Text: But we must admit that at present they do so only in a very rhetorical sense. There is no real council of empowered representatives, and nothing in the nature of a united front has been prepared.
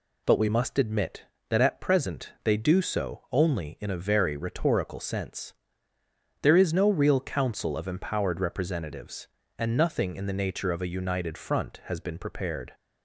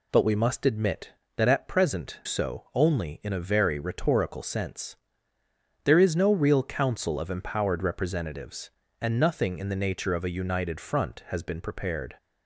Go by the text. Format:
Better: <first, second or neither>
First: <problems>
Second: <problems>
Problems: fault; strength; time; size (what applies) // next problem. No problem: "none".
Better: first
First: none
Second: skips "they do"; at 2.2 s